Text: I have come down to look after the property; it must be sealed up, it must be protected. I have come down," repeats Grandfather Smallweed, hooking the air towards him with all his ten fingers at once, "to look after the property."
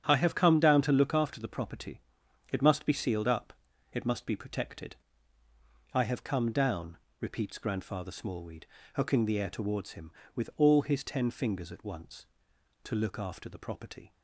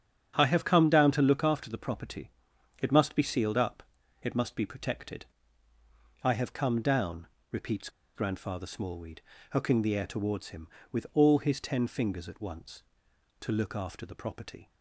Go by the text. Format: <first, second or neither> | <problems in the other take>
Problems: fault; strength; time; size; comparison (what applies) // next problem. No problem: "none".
first | starts louder than the rest; strong; until 1.3 s; 8.5 dB; strong in the first // pauses between "repeats" and "Grandfather"; slight; at 7.8 s; 0.26 s long